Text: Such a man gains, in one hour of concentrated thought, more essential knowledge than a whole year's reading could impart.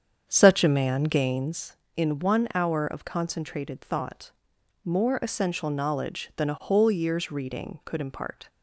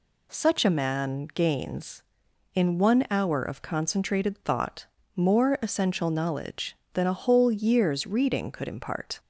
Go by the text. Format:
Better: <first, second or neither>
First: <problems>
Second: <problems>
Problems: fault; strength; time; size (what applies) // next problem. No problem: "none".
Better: second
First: starts louder than the rest; strong; until 1.6 s; 7.5 dB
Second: none